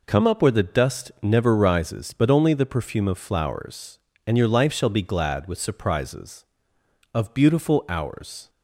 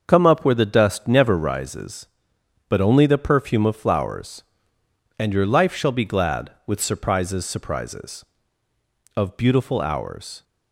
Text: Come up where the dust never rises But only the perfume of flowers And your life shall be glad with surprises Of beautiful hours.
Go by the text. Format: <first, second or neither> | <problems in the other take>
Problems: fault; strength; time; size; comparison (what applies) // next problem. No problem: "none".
first | starts louder than the rest; until 1.0 s; 6.5 dB // says "surprises" twice; at 7.4 s